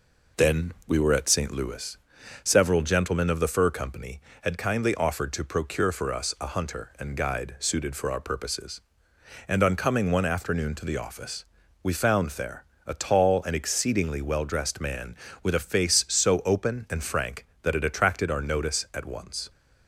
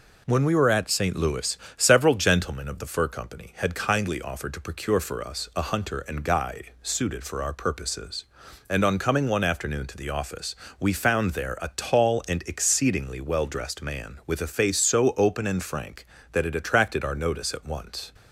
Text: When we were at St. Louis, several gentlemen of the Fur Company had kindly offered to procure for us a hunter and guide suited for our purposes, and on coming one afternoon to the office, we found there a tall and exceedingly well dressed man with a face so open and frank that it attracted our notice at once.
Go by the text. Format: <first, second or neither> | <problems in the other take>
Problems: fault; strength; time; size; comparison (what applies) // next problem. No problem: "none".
second | says "Then" for "When"; at 0.3 s // pauses between "there" and "a"; slight; at 12.6 s; 0.20 s long